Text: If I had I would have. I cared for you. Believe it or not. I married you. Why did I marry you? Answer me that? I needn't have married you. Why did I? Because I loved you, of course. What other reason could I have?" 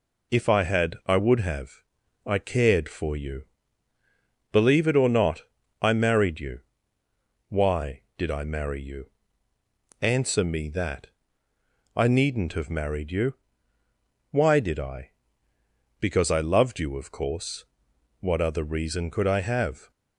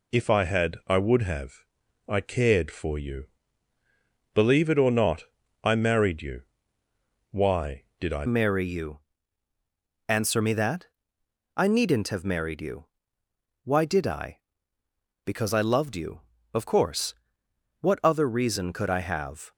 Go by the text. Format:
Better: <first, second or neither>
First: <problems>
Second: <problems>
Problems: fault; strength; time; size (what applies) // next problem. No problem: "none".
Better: first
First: none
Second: changes voice at "marry"; from 8.2 s on; 11.3 s long